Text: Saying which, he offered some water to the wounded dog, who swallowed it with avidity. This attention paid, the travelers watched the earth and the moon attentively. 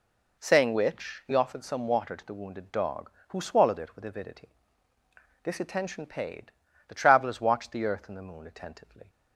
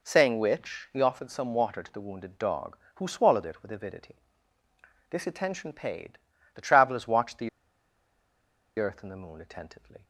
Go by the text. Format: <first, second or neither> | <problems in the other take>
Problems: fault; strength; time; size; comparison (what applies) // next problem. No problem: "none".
first | pauses between "the" and "earth"; strong; at 7.4 s; 1.3 s long